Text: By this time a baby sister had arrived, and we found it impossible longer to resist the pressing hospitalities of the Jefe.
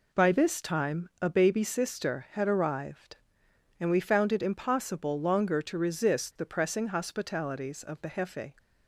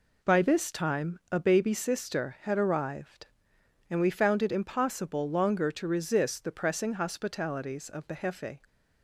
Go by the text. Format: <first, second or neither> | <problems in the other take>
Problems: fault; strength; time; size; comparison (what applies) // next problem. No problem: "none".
neither | none